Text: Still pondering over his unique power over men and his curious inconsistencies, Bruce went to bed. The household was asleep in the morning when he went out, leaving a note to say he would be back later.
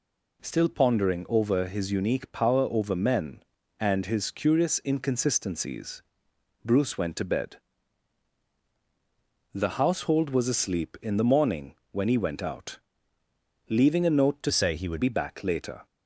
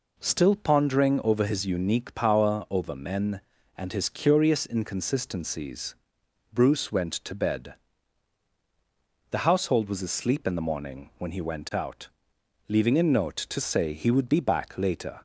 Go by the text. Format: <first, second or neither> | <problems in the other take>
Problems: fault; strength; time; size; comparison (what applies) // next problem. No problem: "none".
second | pauses between "morning" and "when"; slight; at 11.7 s; 0.16 s long // changes voice from "say" to "would"; from 14.5 to 15.0 s; 0.5 s long